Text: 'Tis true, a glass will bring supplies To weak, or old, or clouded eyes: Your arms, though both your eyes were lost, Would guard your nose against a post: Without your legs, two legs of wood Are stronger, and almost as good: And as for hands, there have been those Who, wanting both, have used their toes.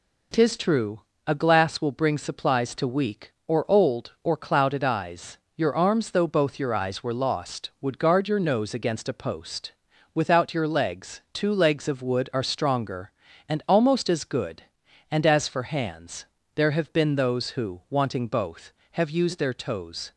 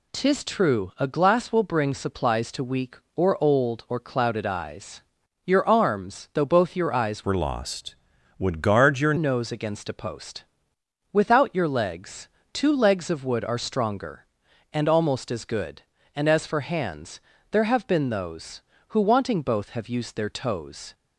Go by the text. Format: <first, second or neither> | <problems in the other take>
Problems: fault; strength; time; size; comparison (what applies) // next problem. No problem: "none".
first | changes voice from "were" to "your"; from 7.2 to 9.1 s; 1.9 s long